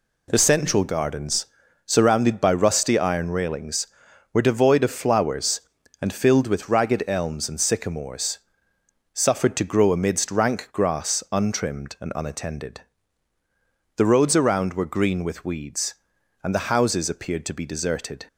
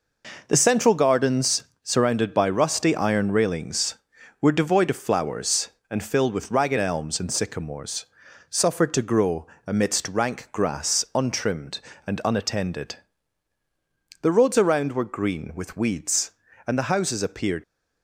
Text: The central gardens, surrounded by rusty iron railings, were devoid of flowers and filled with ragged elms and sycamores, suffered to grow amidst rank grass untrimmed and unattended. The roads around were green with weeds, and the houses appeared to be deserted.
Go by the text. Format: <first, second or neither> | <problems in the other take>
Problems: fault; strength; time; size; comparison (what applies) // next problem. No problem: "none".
first | pauses between "grow" and "amidst"; slight; at 9.4 s; 0.20 s long // stops before "to be deserted"; at 17.6 s